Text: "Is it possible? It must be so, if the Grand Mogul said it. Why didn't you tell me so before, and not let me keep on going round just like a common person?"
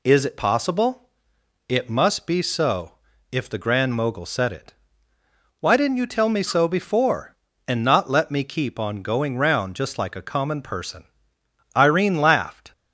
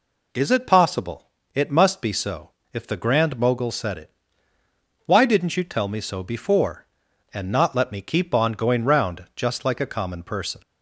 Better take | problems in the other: second | goes on to say "Irene laughed"; noticeable; from 11.7 s on; 0.96 s long

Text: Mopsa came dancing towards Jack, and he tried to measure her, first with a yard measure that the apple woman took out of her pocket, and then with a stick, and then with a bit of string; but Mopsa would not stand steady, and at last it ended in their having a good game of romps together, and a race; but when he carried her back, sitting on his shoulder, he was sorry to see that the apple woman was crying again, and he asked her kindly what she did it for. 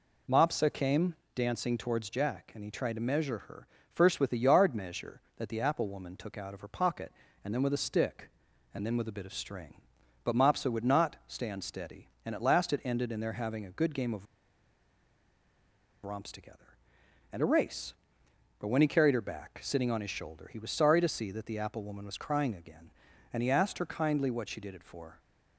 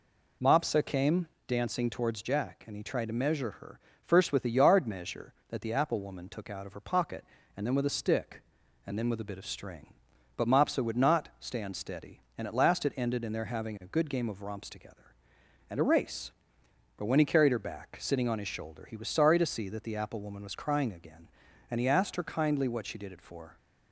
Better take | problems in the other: second | pauses between "came" and "dancing"; slight; at 1.1 s; 0.20 s long; slight in the second // pauses between "of" and "romps"; strong; at 14.2 s; 1.7 s long

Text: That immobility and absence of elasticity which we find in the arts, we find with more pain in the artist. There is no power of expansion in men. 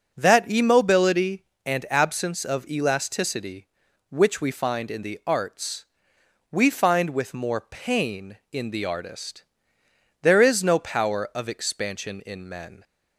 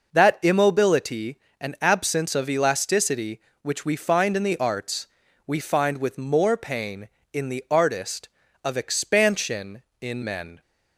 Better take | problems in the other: first | skips "There is no power"; at 8.4 s

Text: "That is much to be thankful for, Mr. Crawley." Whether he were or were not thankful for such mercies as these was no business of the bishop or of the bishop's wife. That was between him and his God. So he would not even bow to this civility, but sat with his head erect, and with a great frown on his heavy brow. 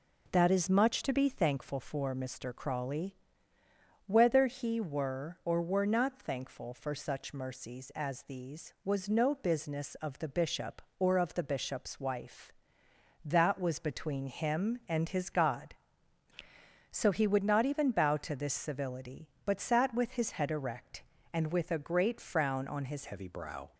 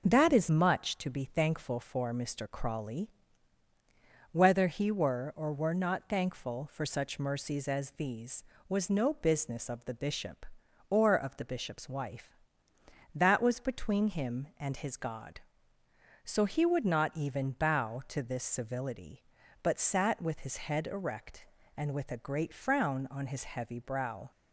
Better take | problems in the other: second | changes voice at "heavy"; from 23.0 s on; 0.7 s long

